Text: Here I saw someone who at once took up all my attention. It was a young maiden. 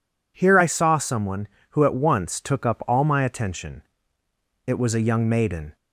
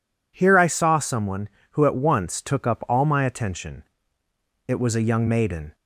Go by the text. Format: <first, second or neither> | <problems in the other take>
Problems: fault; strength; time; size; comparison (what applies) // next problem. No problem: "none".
neither | none